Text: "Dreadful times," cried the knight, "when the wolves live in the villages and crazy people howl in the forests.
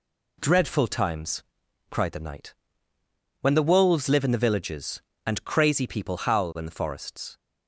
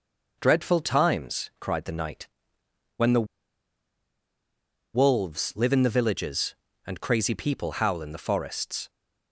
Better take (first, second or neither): first